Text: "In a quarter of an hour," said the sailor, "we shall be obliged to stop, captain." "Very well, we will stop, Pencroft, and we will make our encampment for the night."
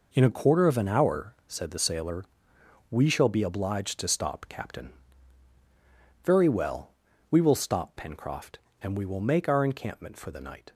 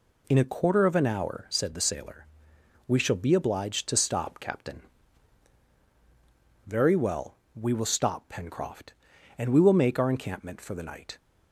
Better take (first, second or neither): neither